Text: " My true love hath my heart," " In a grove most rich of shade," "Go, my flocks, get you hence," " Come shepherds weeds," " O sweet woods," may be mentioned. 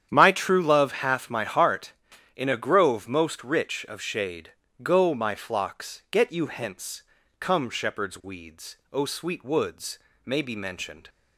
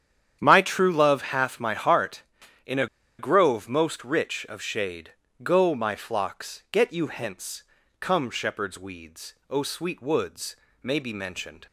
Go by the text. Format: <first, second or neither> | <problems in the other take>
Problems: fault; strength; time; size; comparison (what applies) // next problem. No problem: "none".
first | starts louder than the rest; strong; until 1.4 s; 9.5 dB; strong in the first // pauses between "a" and "grove"; slight; at 2.8 s; 0.33 s long